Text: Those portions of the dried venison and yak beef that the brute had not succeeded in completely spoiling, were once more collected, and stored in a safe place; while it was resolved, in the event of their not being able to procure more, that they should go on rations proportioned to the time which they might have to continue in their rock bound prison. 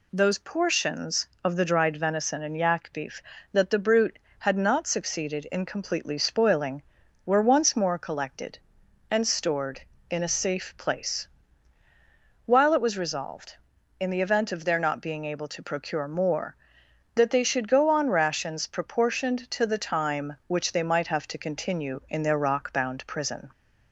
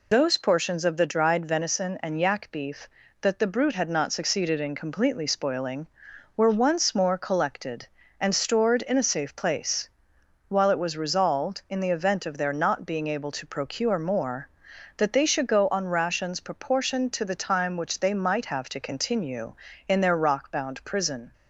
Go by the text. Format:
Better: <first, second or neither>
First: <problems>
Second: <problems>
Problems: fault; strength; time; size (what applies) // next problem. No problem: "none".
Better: first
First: none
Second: loses the start of "Those"; at 0.1 s; 50 ms